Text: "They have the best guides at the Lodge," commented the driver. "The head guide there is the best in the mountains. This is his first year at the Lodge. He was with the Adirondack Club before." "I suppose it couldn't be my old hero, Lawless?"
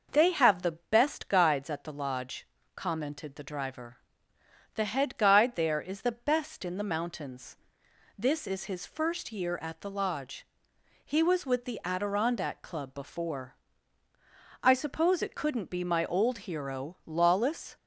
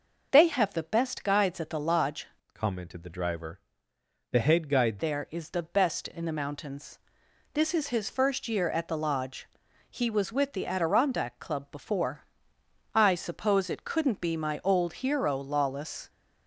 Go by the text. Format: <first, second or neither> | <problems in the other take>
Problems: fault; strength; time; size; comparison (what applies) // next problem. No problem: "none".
first | changes voice from "commented" to "guide"; from 2.5 to 4.9 s; 2.4 s long